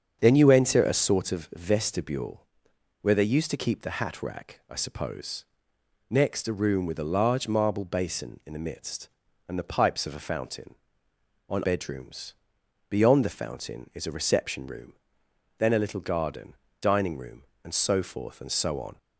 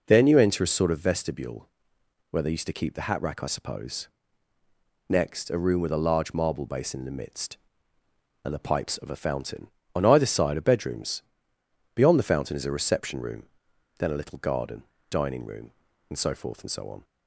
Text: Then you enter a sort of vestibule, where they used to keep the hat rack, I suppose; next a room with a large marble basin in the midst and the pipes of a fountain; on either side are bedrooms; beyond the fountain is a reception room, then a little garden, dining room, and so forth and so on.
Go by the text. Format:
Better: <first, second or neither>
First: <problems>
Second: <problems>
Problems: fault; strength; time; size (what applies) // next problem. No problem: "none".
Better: second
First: starts louder than the rest; strong; until 1.2 s; 7 dB // skips "either side are"; at 11.6 s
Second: none